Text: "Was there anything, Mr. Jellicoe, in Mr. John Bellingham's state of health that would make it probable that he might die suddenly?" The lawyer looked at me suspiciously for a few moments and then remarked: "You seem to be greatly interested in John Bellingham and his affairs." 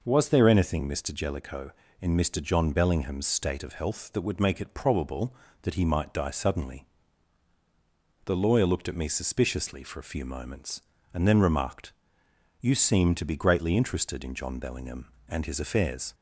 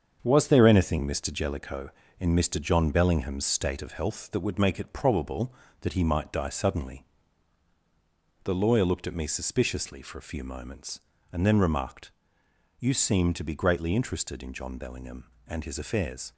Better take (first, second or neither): first